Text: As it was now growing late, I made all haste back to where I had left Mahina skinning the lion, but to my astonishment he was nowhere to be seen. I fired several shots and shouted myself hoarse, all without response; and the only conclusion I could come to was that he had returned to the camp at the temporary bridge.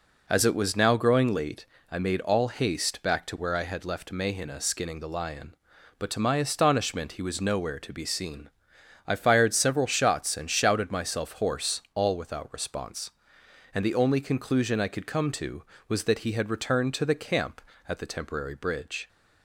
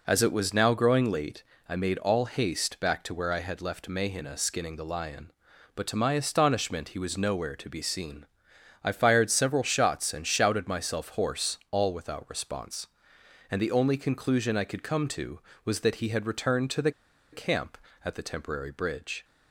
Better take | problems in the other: first | pauses between "the" and "camp"; at 16.9 s; 0.42 s long

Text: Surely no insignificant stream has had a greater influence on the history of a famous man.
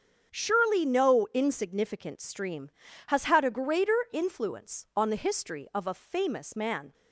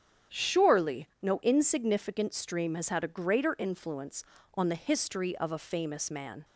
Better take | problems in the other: neither | starts louder than the rest; strong; the same in both

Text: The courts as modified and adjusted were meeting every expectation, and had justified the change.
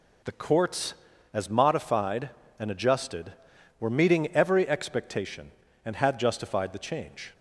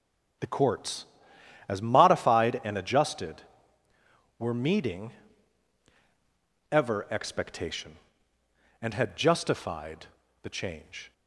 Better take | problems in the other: first | starts louder than the rest; until 2.0 s; 7 dB // says "ever" for "every"; at 6.7 s // pauses between "justified" and "the"; slight; at 10.0 s; 0.36 s long

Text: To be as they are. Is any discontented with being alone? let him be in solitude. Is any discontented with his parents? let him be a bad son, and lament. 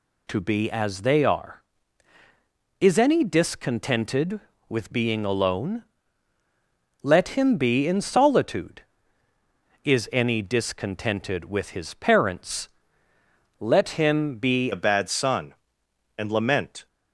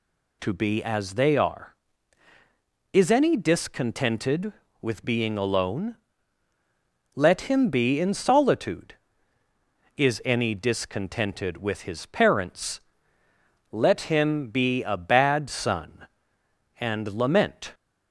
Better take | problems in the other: second | changes voice at "a"; from 14.7 s on; 2.1 s long

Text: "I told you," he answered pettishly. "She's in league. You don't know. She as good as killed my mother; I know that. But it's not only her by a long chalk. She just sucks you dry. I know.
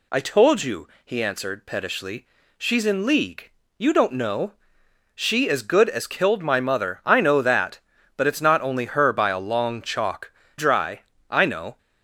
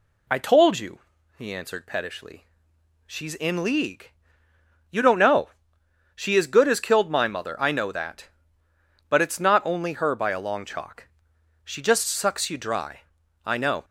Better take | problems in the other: second | skips "She just sucks you"; at 10.4 s

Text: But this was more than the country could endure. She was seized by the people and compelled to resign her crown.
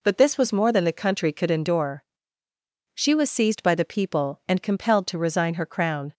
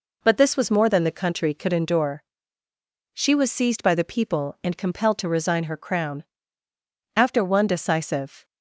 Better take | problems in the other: first | goes on to say "After one decisive"; noticeable; from 7.1 s on; 1.2 s long

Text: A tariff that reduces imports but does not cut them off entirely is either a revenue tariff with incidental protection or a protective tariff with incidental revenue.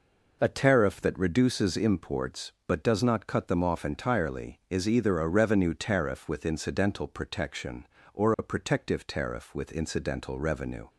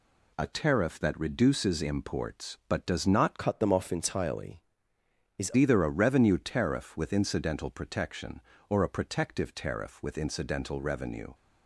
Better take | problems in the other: first | changes voice from "cut" to "is"; from 3.3 to 5.5 s; 2.2 s long

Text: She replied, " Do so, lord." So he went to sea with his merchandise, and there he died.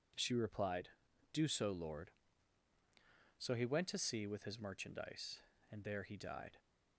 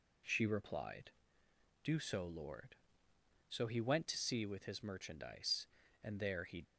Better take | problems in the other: first | stops before "died"; at 6.6 s

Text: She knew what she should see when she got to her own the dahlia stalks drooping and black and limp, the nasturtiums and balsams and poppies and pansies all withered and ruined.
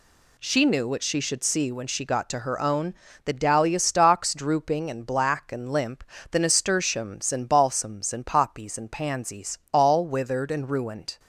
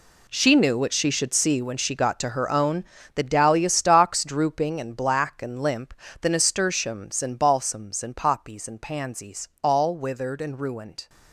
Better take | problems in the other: first | gets quieter; strong; throughout; 13 dB // pauses between "own" and "the"; slight; at 2.8 s; 0.30 s long; slight in the first // pauses between "pansies" and "all"; slight; at 9.4 s; 0.16 s long; slight in the first

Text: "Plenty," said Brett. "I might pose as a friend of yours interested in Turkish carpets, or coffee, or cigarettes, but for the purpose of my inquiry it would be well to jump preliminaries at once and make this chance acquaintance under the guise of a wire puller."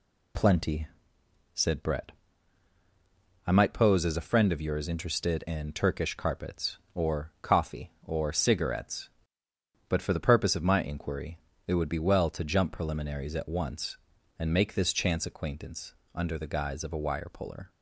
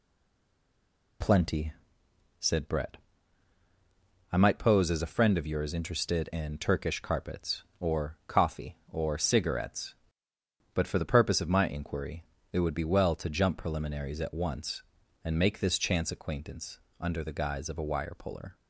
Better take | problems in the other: first | stays silent before the first word; noticeable; until 1.2 s; 1.2 s long // pauses between "inquiry" and "it"; slight; at 12.2 s; 0.28 s long; slight in the first // pauses between "acquaintance" and "under"; slight; at 16.7 s; 0.20 s long; slight in the first

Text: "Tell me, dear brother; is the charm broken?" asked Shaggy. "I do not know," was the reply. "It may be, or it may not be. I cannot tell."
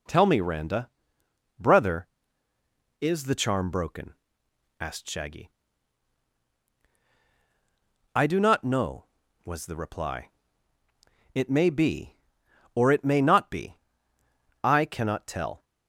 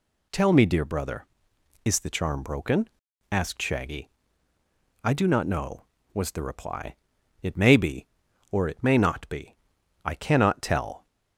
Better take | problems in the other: second | says "randa" for "dear"; at 0.4 s

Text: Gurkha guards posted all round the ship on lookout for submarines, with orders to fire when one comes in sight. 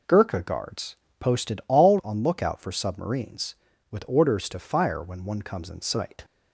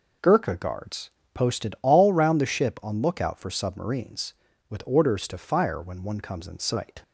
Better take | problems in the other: second | pauses between "guards" and "posted"; slight; at 0.9 s; 0.22 s long; slight in the second // skips "round the ship"; at 2.0 s

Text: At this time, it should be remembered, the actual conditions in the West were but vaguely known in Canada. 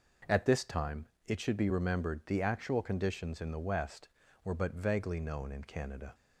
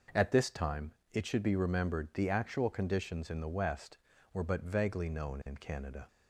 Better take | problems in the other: neither | none

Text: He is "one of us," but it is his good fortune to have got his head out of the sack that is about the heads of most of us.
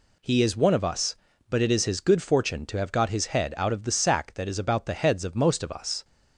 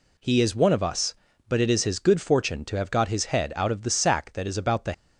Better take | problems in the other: first | stops before "heads of most of us"; at 4.9 s

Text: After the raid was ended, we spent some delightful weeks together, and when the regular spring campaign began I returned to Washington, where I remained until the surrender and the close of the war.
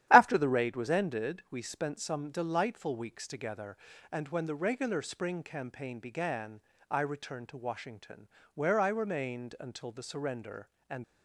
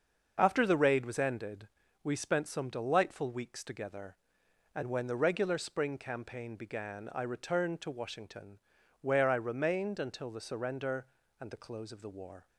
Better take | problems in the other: second | starts louder than the rest; strong; until 1.1 s; 12 dB; also in the second // pauses between "began" and "I"; slight; at 6.6 s; 0.28 s long // stops before "the close of the war"; at 11.0 s

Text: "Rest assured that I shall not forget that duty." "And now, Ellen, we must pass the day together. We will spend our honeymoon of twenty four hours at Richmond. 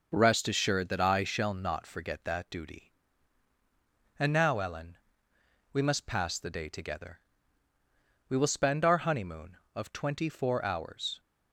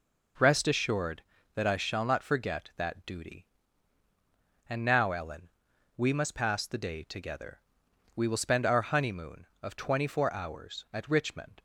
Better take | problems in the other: second | stops before "at Richmond"; at 11.1 s

